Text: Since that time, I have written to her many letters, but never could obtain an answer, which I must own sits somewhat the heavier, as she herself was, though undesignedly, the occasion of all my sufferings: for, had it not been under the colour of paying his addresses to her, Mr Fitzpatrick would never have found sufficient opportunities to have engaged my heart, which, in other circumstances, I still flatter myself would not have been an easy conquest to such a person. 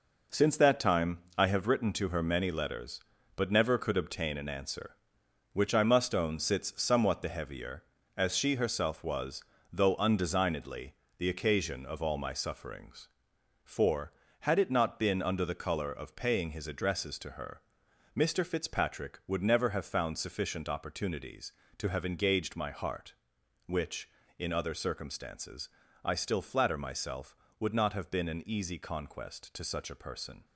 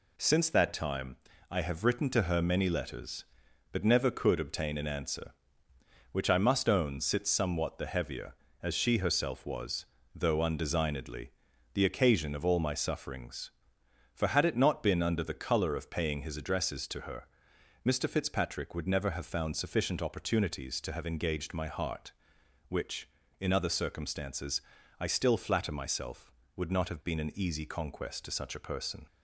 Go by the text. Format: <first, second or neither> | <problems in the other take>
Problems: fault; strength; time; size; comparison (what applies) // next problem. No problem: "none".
second | gets quieter; strong; throughout; 8.5 dB